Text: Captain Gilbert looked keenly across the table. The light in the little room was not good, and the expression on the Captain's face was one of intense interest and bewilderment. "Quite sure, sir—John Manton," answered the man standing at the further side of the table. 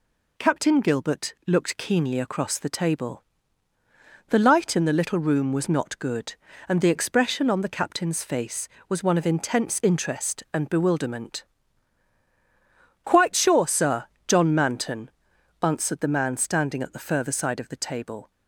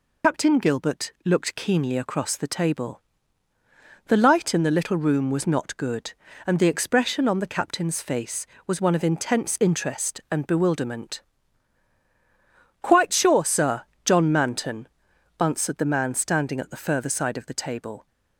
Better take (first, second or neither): first